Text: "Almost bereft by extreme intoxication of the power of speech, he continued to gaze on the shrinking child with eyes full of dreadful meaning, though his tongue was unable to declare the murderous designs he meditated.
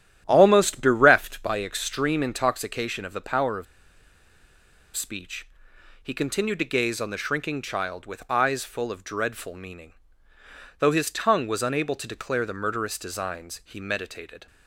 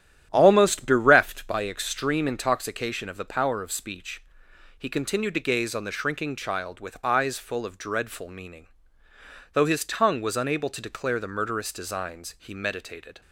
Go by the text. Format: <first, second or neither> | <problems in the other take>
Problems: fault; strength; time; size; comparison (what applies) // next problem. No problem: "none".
second | starts louder than the rest; strong; until 1.2 s; 10.5 dB; strong in the second // pauses between "of" and "speech"; strong; at 3.6 s; 1.3 s long